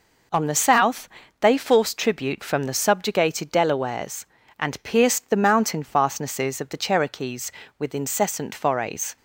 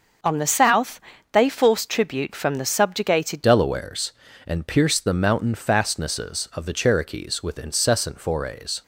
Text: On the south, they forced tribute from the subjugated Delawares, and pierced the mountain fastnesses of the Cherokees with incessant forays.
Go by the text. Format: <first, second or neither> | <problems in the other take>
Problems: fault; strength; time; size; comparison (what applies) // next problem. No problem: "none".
first | starts louder than the rest; until 1.5 s; 6 dB // changes voice at "Delawares"; from 3.4 s on; 5.4 s long